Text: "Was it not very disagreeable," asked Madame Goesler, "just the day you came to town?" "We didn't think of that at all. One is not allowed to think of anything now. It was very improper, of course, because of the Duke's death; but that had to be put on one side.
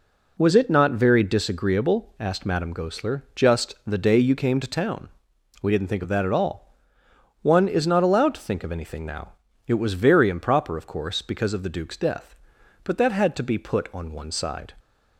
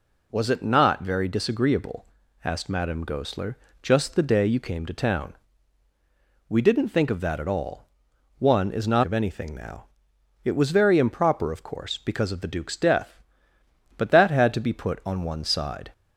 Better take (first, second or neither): first